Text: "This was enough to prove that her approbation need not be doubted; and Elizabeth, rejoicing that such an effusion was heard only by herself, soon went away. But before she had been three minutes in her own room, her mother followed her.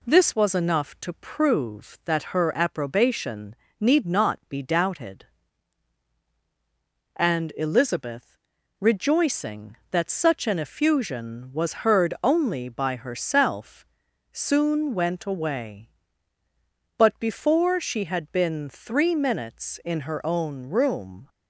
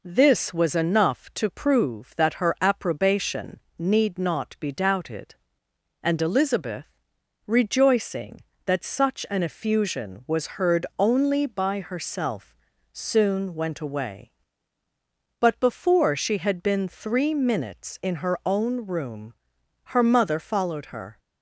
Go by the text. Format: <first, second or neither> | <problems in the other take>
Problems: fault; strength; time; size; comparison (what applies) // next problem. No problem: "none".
second | pauses between "approbation" and "need"; slight; at 3.5 s; 0.24 s long; slight in the second // stops before "her mother followed her"; at 21.2 s